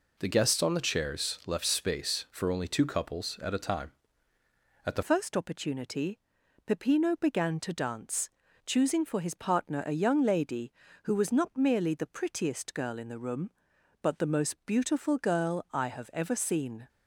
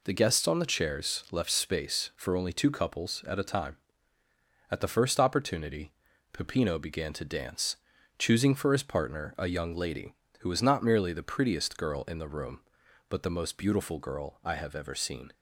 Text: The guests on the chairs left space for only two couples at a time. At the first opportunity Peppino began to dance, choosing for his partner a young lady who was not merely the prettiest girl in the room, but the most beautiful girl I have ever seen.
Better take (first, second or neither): second